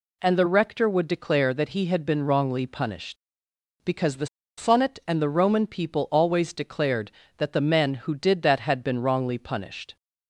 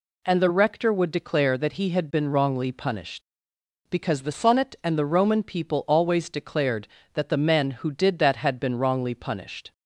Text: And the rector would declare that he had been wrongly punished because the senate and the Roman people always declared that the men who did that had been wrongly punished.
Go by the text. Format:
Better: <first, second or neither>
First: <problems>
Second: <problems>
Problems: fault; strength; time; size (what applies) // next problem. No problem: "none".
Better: second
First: pauses between "the" and "senate"; slight; at 4.2 s; 0.30 s long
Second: none